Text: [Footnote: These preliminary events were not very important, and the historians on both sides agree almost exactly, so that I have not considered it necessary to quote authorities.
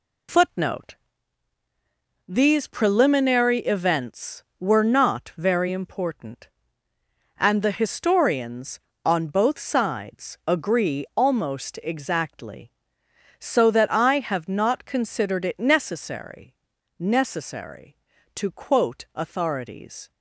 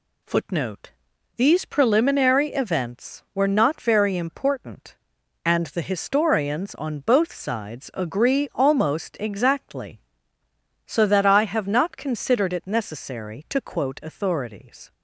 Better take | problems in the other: second | says "necessary" twice; at 16.9 s

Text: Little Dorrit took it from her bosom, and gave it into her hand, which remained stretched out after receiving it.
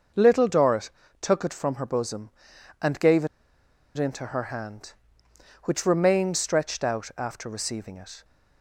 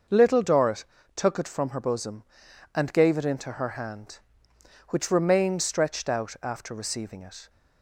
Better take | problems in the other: second | starts louder than the rest; noticeable; until 1.4 s; 6 dB; noticeable in the second // pauses between "Dorrit" and "took"; slight; at 0.9 s; 0.32 s long; slight in the second // pauses between "gave" and "it"; noticeable; at 3.2 s; 0.70 s long

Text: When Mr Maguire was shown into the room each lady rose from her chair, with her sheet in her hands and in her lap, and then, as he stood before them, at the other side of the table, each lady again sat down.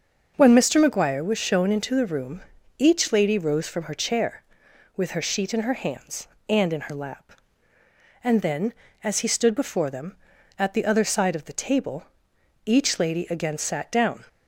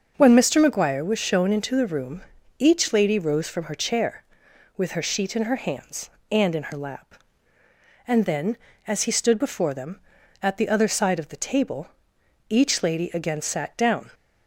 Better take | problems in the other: neither | starts louder than the rest; the same in both // pauses between "room" and "each"; the same in both

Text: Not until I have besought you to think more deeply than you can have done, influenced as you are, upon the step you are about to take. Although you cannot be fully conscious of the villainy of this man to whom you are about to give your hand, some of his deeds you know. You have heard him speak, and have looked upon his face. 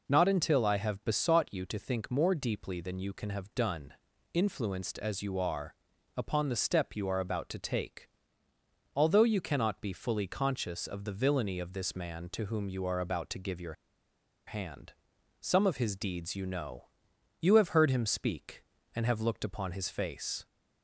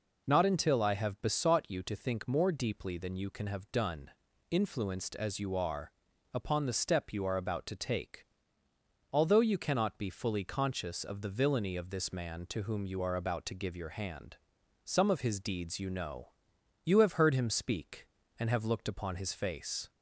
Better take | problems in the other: second | pauses between "your" and "hand"; noticeable; at 13.7 s; 0.73 s long

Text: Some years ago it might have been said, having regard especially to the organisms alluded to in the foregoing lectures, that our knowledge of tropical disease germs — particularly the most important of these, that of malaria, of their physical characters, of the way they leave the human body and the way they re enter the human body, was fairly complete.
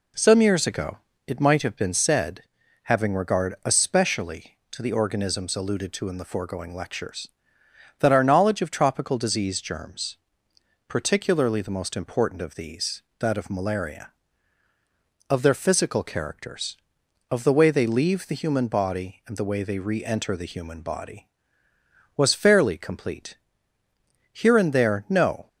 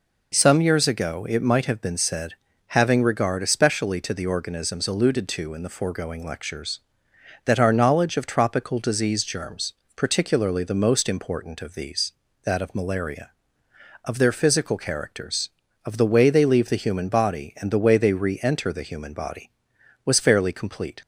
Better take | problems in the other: second | pauses between "ago" and "it"; slight; at 0.9 s; 0.28 s long // goes on to say "Here and there no"; noticeable; from 24.4 s on; 1.0 s long

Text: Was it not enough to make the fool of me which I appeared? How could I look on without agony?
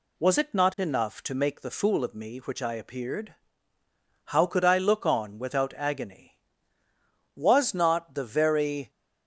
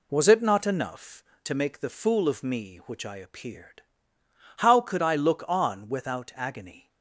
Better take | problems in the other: second | goes on to say "Was not the very"; from 7.3 s on; 1.5 s long

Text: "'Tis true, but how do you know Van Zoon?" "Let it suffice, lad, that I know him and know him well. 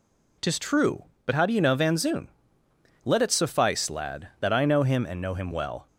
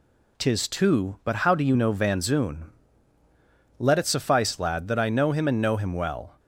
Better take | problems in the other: first | says "two" for "true"; at 0.6 s

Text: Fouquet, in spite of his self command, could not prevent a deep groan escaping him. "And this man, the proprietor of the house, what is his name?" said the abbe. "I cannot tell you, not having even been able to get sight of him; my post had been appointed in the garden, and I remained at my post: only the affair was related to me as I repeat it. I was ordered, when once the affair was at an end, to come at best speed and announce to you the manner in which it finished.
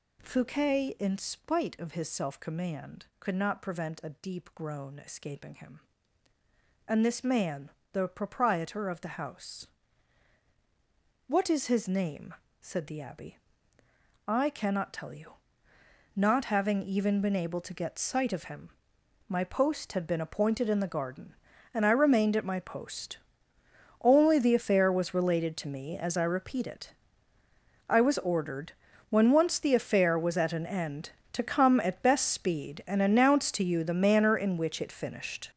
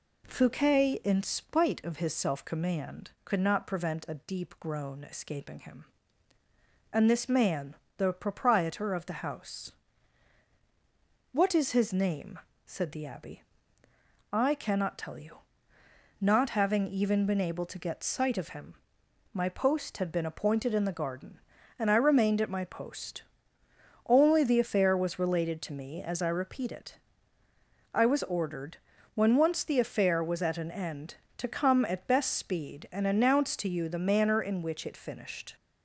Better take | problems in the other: second | gets louder; strong; throughout; 10 dB

